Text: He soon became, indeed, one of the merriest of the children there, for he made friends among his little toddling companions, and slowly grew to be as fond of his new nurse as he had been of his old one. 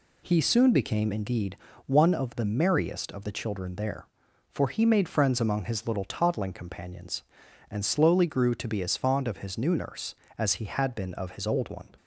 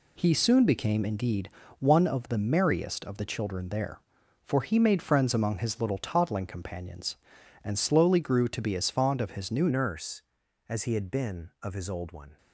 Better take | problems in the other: first | changes voice at "nurse"; from 9.6 s on; 2.7 s long

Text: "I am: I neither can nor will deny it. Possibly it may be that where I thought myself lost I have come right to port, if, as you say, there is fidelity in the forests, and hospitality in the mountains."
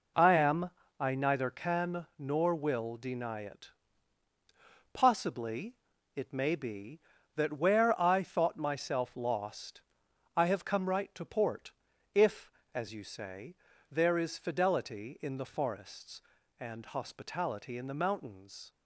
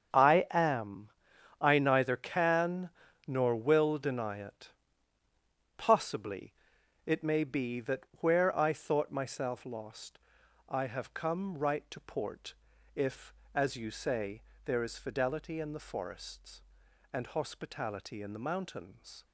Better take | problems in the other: first | gets quieter; strong; throughout; 12.5 dB // pauses between "can" and "nor"; at 2.8 s; 0.38 s long // pauses between "Possibly" and "it"; noticeable; at 6.5 s; 0.50 s long; also in the first // pauses between "lost" and "I"; noticeable; at 10.1 s; 0.48 s long; noticeable in the first

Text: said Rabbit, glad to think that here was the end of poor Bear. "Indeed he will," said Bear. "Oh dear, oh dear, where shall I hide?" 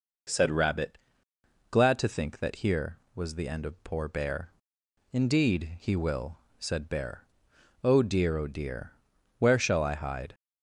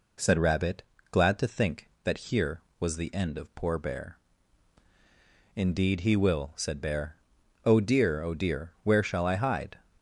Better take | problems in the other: neither | none

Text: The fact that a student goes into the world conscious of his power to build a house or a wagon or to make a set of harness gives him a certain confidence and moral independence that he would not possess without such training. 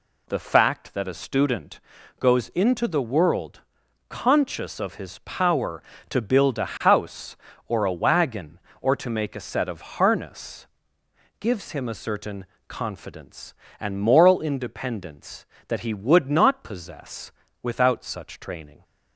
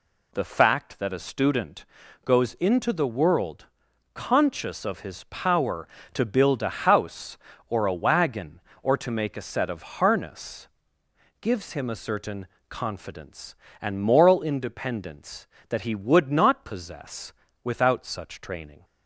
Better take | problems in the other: neither | pauses between "student" and "goes"; the same in both // pauses between "world" and "conscious"; noticeable; the same in both // pauses between "harness" and "gives"; noticeable; the same in both // pauses between "certain" and "confidence"; slight; the same in both // pauses between "possess" and "without"; slight; the same in both

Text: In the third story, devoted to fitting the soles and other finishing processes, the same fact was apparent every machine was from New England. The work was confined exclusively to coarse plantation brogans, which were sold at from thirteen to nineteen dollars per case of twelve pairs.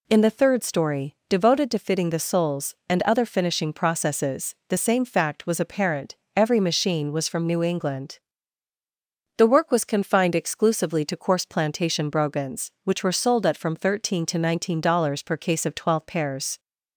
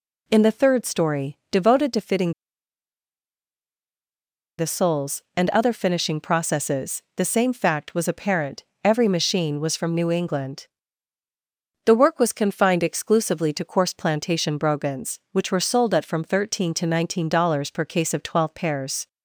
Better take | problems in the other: first | pauses between "fitting" and "the"; strong; at 2.3 s; 2.2 s long // pauses between "apparent" and "every"; slight; at 8.6 s; 0.20 s long; slight in the first

